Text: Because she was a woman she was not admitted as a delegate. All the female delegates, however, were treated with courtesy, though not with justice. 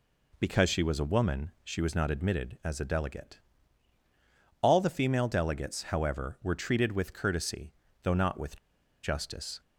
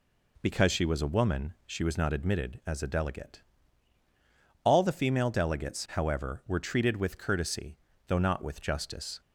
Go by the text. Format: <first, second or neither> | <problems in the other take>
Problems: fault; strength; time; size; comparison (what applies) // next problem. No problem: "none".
second | pauses between "with" and "justice"; noticeable; at 8.5 s; 0.47 s long